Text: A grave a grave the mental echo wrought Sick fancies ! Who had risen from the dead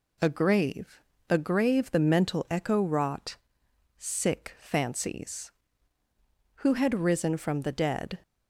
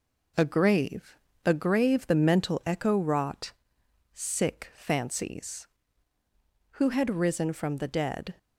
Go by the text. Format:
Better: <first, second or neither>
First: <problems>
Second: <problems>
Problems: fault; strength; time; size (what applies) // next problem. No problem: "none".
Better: first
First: pauses between "grave" and "a"; slight; at 0.9 s; 0.30 s long // pauses between "wrought" and "Sick"; noticeable; at 3.3 s; 0.62 s long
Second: gets quieter; throughout; 4 dB // pauses between "grave" and "a"; slight; at 1.1 s; 0.30 s long // pauses between "wrought" and "Sick"; noticeable; at 3.5 s; 0.62 s long